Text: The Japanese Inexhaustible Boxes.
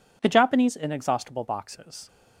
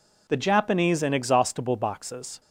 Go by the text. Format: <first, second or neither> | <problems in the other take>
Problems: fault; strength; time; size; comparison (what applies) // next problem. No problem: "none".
neither | none